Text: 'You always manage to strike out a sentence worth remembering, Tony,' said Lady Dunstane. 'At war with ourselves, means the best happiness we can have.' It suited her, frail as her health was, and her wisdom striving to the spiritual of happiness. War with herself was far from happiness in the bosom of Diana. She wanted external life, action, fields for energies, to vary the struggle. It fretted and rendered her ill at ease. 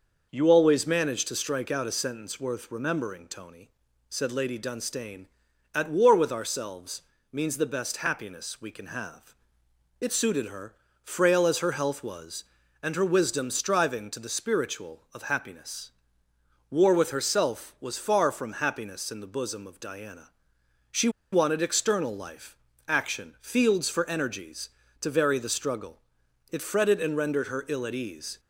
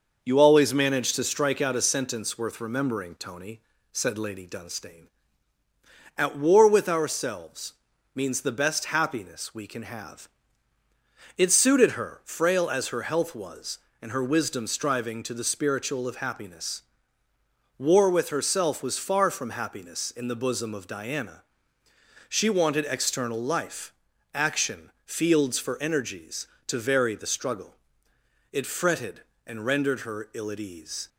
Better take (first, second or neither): second